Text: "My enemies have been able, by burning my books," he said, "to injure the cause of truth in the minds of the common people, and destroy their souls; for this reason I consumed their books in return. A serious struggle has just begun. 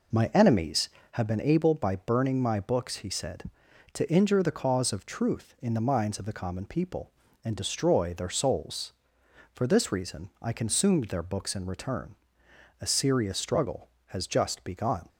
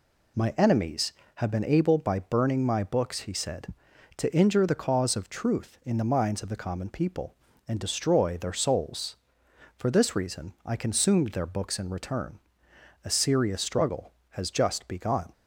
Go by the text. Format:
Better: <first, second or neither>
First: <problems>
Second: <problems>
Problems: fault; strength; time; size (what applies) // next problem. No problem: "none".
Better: second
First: starts louder than the rest; noticeable; until 1.3 s; 4 dB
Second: none